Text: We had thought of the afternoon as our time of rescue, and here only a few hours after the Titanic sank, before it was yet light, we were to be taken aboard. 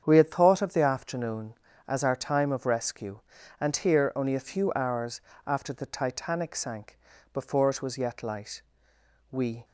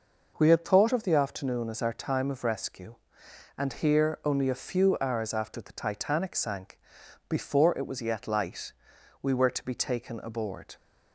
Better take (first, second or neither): second